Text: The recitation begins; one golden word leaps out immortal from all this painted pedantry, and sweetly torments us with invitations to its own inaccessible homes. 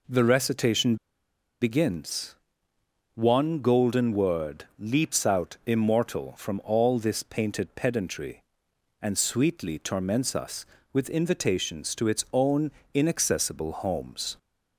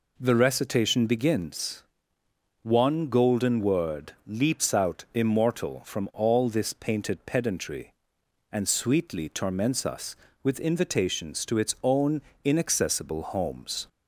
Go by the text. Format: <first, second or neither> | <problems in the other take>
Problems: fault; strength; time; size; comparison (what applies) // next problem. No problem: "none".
second | pauses between "recitation" and "begins"; noticeable; at 0.9 s; 0.65 s long // pauses between "own" and "inaccessible"; slight; at 12.6 s; 0.24 s long; slight in the second